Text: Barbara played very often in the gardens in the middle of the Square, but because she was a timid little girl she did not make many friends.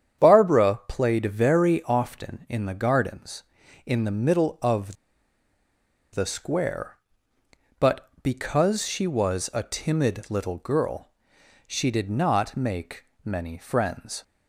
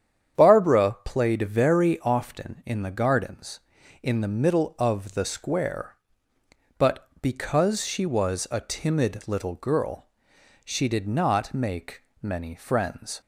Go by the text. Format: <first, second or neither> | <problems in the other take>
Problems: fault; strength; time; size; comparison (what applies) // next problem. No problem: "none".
second | starts louder than the rest; strong; until 1.2 s; 8.5 dB; strong in the second // pauses between "of" and "the"; at 4.9 s; 1.1 s long // pauses between "girl" and "she"; noticeable; at 11.1 s; 0.58 s long; noticeable in the second // pauses between "make" and "many"; slight; at 13.0 s; 0.20 s long; slight in the second